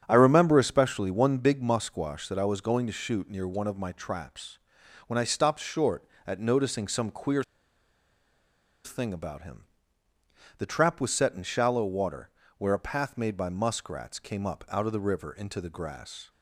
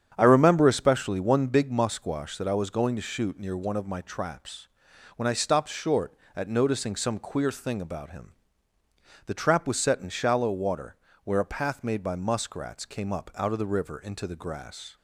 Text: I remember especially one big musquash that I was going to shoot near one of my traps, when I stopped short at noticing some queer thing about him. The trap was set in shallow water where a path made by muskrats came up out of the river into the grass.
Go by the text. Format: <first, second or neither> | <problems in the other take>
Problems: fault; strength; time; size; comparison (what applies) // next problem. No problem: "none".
second | starts louder than the rest; strong; until 1.0 s; 8.5 dB; strong in the second // pauses between "queer" and "thing"; strong; at 7.4 s; 1.4 s long // pauses between "water" and "where"; slight; at 12.2 s; 0.30 s long; slight in the second